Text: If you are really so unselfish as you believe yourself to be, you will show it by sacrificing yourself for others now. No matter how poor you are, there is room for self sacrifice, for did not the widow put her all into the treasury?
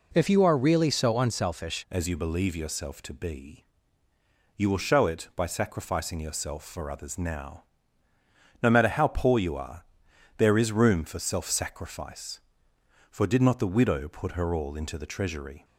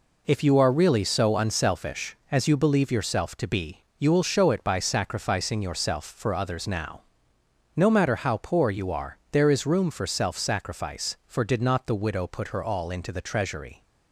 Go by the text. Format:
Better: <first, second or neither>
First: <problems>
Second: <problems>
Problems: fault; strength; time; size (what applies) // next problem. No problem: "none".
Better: second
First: changes voice at "as"; from 1.8 s on; 13.8 s long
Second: none